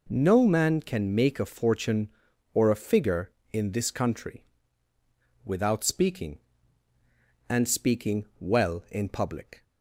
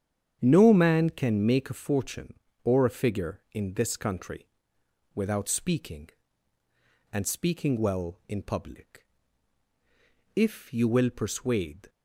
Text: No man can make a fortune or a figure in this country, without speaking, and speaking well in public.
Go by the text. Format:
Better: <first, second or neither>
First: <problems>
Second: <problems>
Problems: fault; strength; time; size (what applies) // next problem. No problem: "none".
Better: first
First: none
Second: starts louder than the rest; strong; until 1.4 s; 8.5 dB // goes on to say "If you will persuade"; from 10.3 s on; 1.5 s long